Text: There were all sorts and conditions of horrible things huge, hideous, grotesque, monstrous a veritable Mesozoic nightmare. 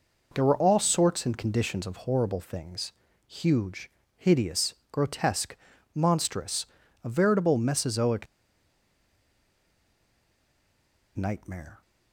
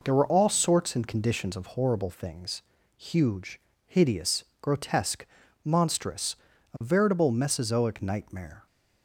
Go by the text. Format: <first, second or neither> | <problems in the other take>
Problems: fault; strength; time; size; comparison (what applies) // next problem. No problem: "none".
second | pauses between "things" and "huge"; slight; at 2.9 s; 0.34 s long; slight in the second // pauses between "monstrous" and "a"; at 6.6 s; 0.38 s long; also in the second // pauses between "Mesozoic" and "nightmare"; strong; at 8.2 s; 2.9 s long